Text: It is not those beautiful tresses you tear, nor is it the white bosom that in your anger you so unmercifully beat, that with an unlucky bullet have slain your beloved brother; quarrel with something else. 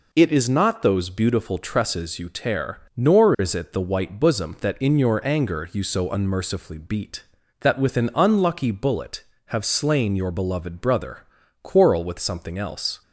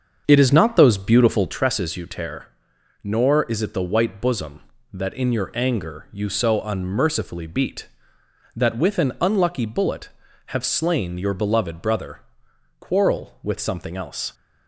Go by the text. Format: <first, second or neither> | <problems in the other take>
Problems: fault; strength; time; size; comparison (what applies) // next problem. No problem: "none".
first | starts louder than the rest; until 1.6 s; 7 dB